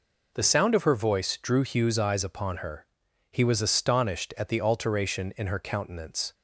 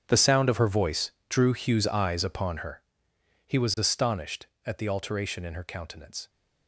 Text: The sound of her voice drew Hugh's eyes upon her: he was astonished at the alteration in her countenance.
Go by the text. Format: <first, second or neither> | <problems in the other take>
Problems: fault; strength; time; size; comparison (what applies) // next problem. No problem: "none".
first | gets quieter; strong; throughout; 16.5 dB // pauses between "voice" and "drew"; slight; at 1.1 s; 0.16 s long